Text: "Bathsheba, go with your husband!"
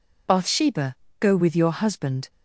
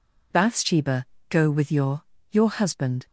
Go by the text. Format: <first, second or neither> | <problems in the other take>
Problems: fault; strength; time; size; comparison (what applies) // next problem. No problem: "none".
first | says "your" twice; at 2.2 s